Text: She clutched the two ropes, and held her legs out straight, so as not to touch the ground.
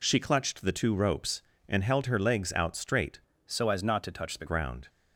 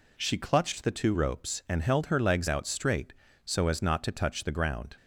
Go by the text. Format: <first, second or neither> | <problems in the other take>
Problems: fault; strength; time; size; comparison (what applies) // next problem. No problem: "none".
second | changes voice from "so" to "the"; from 3.4 to 4.4 s; 1.0 s long